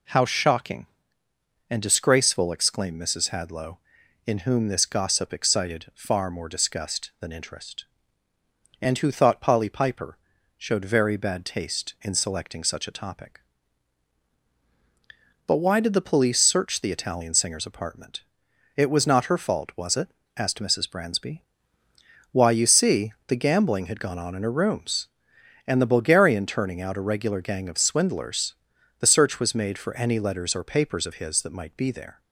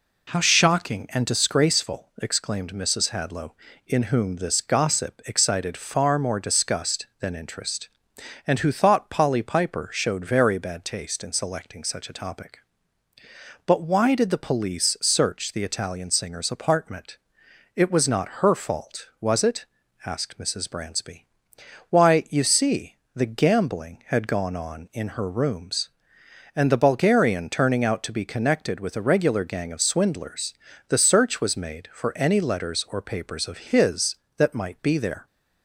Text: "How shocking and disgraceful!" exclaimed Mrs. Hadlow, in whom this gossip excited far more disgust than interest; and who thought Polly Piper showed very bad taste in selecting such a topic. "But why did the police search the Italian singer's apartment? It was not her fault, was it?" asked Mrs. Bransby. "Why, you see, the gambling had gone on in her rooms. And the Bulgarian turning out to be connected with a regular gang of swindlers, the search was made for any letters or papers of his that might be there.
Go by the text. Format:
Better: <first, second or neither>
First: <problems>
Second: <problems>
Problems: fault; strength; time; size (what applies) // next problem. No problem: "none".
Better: second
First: pauses between "Piper" and "showed"; at 10.1 s; 0.40 s long // skips "to be connected with"; at 26.9 s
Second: none